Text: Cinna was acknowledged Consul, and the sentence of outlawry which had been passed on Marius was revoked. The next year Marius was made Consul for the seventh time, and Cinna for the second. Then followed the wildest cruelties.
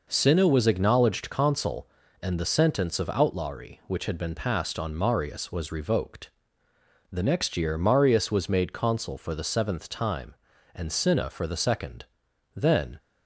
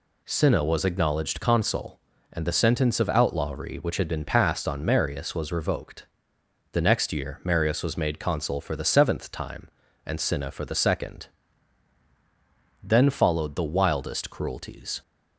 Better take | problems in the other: second | stops before "followed the wildest cruelties"; at 12.9 s

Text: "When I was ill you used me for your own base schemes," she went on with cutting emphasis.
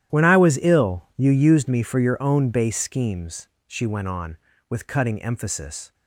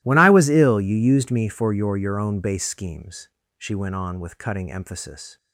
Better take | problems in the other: first | starts louder than the rest; strong; until 1.0 s; 16.5 dB; strong in the first // says "your" twice; at 1.9 s

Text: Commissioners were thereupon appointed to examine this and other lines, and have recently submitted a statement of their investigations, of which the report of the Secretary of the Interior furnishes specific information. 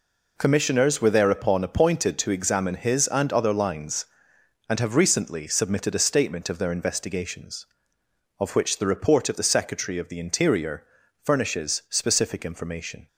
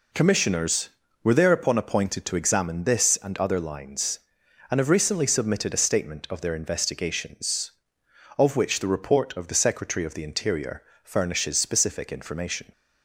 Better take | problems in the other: second | says "his" for "this"; at 2.7 s // pauses between "Interior" and "furnishes"; at 10.8 s; 0.38 s long; slight in the second

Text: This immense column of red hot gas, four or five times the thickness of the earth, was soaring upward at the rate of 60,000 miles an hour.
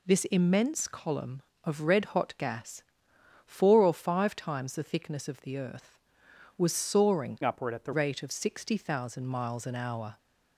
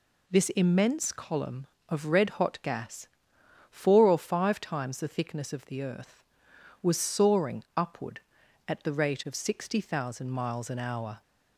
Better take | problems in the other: second | changes voice from "upward" to "the"; from 7.4 to 7.9 s; 0.5 s long

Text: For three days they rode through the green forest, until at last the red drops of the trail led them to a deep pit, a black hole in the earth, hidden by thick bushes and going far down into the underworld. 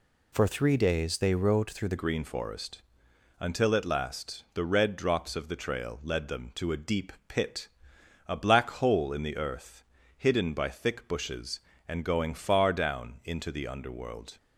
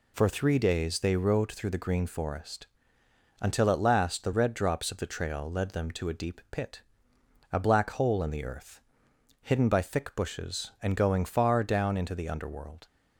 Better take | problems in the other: second | changes voice at "green"; from 1.9 s on; 12.4 s long // pauses between "deep" and "pit"; slight; at 7.1 s; 0.16 s long

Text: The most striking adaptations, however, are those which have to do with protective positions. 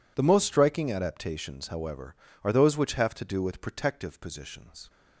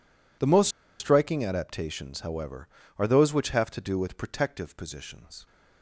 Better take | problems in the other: first | pauses between "most" and "striking"; slight; at 0.6 s; 0.31 s long

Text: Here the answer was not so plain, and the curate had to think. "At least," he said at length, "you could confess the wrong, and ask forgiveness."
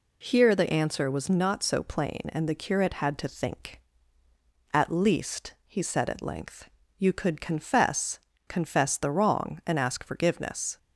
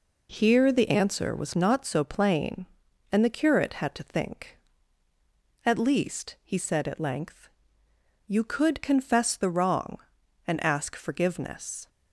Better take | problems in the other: second | says "confess" twice; at 8.4 s

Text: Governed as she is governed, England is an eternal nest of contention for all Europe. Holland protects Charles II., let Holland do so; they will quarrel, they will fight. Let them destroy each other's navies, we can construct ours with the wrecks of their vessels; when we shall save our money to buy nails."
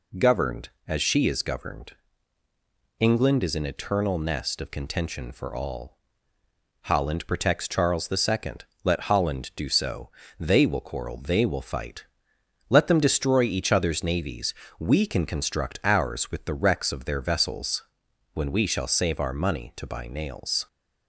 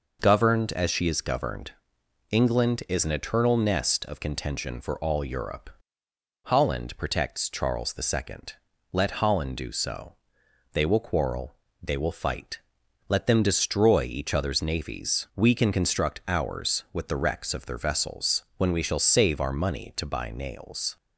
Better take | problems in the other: second | skips "Europe"; at 6.4 s

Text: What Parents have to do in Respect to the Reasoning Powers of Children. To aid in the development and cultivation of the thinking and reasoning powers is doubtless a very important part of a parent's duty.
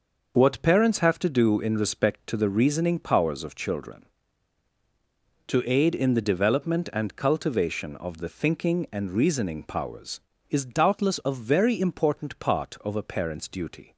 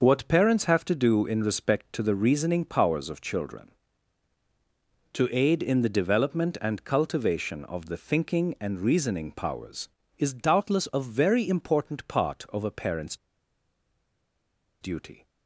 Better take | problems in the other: first | pauses between "parent's" and "duty"; strong; at 13.1 s; 1.6 s long

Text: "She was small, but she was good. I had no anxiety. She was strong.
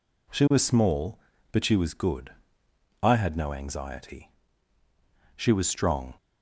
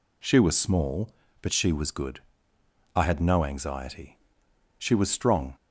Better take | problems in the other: neither | none

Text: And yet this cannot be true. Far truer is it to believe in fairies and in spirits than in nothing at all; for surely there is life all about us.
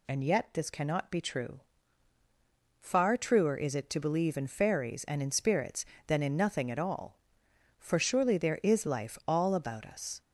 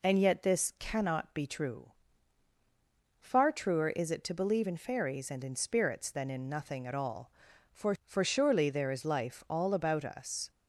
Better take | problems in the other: first | says "for" twice; at 8.0 s

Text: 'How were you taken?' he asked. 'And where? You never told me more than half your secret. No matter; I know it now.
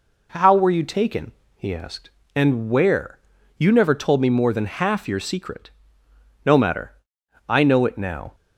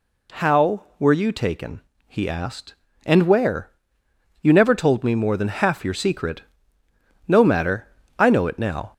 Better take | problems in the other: first | gets louder; slight; throughout; 2.5 dB

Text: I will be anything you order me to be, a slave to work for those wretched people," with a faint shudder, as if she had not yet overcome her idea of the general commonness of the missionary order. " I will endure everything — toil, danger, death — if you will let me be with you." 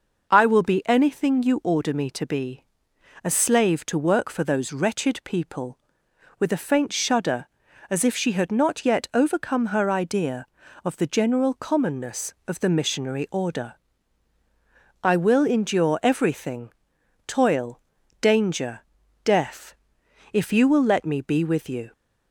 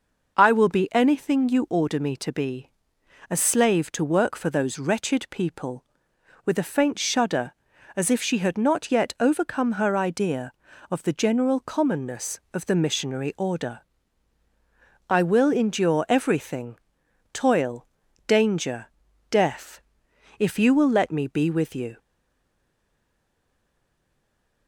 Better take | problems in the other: first | stays silent after the last word; strong; from 21.9 s on; 2.7 s long

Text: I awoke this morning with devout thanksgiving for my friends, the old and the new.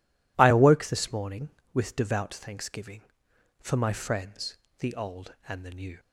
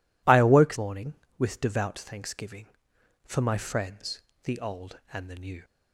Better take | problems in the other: first | skips "this"; at 0.7 s

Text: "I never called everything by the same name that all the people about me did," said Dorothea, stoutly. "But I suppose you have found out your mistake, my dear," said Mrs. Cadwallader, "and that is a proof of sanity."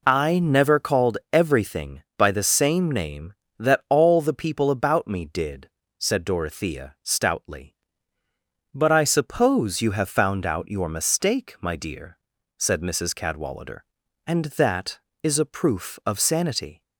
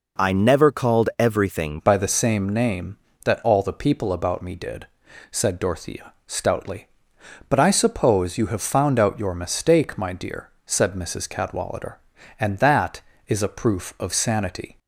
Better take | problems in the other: first | changes voice at "by"; from 1.8 s on; 12.9 s long

